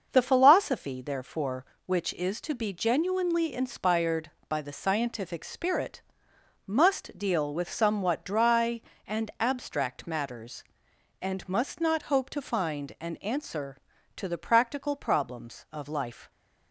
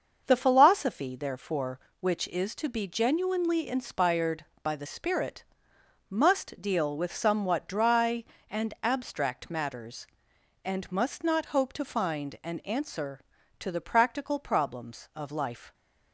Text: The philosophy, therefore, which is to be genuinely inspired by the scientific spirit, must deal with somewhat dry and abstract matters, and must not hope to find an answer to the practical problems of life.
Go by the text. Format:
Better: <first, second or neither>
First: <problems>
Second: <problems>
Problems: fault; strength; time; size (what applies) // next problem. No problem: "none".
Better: first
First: starts louder than the rest; until 1.1 s; 6.5 dB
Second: starts louder than the rest; until 1.2 s; 6.5 dB // skips "scientific"; at 4.8 s